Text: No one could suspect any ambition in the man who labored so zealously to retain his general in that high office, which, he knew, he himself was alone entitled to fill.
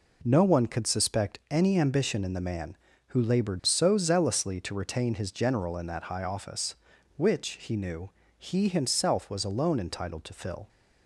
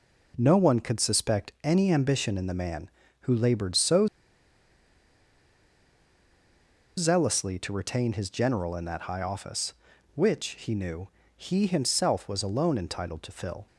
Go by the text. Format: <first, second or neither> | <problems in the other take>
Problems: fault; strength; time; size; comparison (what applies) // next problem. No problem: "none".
first | pauses between "so" and "zealously"; strong; at 4.0 s; 2.9 s long